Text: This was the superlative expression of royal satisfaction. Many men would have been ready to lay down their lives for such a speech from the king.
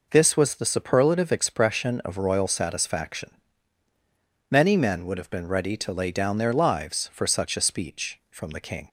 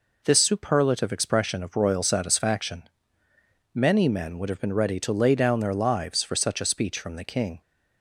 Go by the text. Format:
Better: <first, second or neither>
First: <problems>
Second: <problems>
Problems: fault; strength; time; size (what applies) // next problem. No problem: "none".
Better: first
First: none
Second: skips "was the"; at 0.3 s